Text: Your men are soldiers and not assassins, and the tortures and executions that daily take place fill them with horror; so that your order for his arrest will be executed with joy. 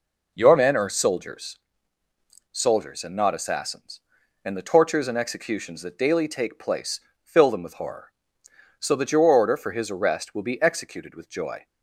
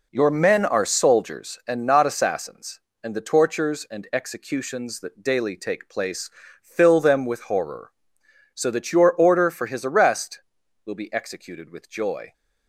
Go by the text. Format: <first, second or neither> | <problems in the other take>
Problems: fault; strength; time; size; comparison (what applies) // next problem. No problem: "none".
second | says "soldiers" twice; at 2.5 s // pauses between "place" and "fill"; slight; at 7.0 s; 0.22 s long; slight in the second